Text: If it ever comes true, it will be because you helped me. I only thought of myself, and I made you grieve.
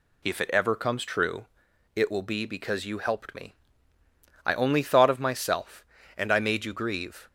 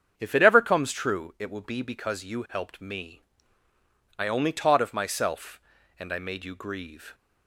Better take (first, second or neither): first